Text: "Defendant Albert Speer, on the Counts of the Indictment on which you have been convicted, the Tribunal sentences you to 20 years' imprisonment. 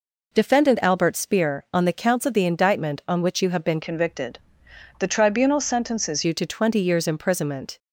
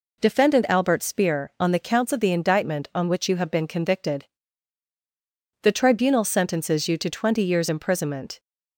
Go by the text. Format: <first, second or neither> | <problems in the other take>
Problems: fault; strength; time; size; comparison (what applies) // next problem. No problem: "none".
second | changes voice from "convicted" to "sentences"; from 3.8 to 6.2 s; 2.4 s long